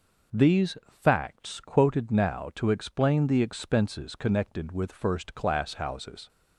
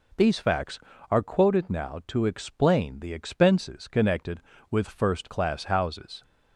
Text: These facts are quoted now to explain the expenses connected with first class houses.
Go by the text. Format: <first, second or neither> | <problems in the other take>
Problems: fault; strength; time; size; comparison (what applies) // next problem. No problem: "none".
second | pauses between "These" and "facts"; slight; at 0.7 s; 0.24 s long // skips "are"; at 1.5 s